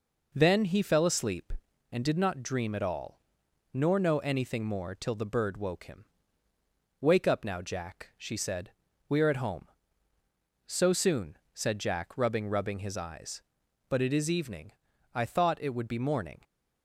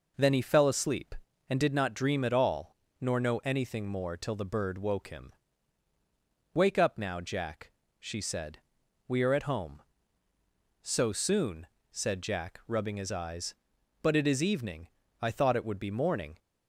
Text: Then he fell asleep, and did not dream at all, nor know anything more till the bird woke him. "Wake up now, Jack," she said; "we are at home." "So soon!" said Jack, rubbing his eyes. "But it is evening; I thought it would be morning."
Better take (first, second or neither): second